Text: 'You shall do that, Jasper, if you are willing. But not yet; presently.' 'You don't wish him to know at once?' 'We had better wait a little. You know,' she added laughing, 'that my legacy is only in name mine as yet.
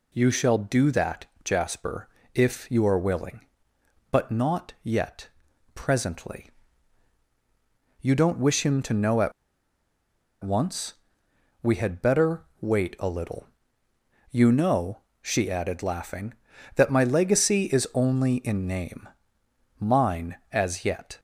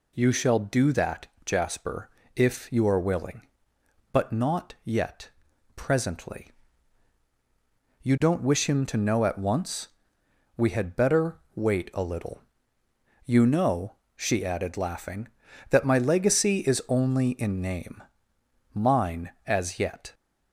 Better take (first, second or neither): second